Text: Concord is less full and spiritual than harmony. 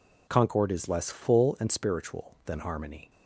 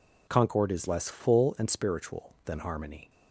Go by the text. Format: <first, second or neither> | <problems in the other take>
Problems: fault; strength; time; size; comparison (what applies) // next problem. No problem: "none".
neither | none